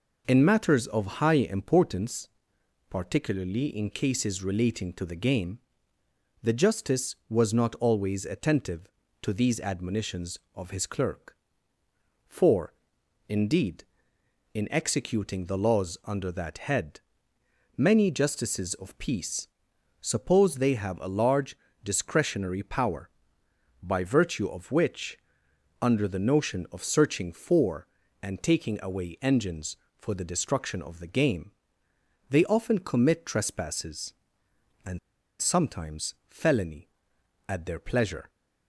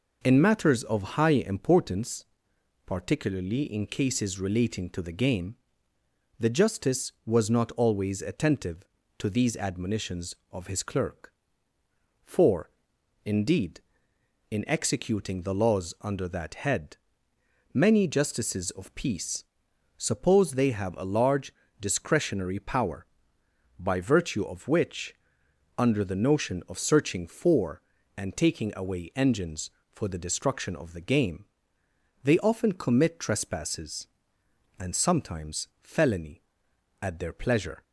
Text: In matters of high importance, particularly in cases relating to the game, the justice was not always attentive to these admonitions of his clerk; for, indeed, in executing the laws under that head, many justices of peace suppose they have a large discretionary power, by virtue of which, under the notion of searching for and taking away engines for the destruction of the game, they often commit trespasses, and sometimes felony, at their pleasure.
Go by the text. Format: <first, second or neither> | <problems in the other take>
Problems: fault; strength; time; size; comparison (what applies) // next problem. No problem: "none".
second | pauses between "peace" and "suppose"; noticeable; at 19.4 s; 0.54 s long; noticeable in the second // pauses between "large" and "discretionary"; slight; at 21.5 s; 0.28 s long; slight in the second // pauses between "and" and "sometimes"; at 34.9 s; 0.42 s long // pauses between "sometimes" and "felony"; slight; at 36.1 s; 0.16 s long; slight in the second